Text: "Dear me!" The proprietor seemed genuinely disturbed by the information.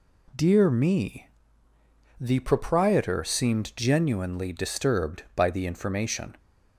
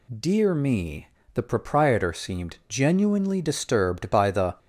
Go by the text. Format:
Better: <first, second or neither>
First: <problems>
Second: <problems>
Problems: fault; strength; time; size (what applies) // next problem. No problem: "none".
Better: first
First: none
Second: stops before "information"; at 4.5 s